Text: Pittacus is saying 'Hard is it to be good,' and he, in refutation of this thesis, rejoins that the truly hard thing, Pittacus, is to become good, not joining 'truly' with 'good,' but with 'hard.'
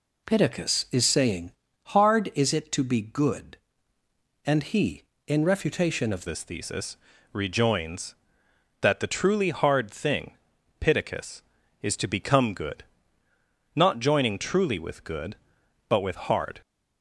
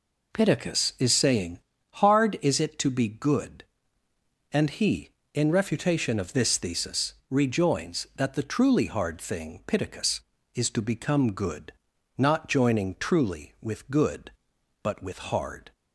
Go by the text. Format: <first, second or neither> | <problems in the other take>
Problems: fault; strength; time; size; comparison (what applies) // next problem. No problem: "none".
second | pauses between "saying" and "Hard"; slight; at 1.5 s; 0.36 s long; slight in the second // changes voice at "this"; from 6.2 s on; 10.4 s long